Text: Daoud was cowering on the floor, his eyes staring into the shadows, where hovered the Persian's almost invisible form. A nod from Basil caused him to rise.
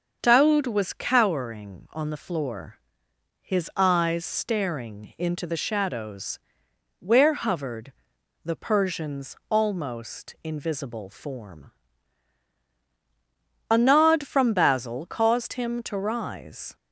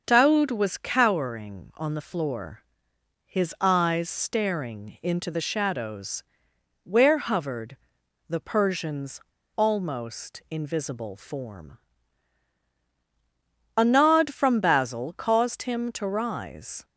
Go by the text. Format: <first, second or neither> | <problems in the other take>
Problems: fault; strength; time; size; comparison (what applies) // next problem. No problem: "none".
first | starts louder than the rest; until 1.0 s; 6.5 dB; also in the first // pauses between "hovered" and "the"; noticeable; at 7.7 s; 0.52 s long; noticeable in the first // pauses between "Persian's" and "almost"; slight; at 9.1 s; 0.34 s long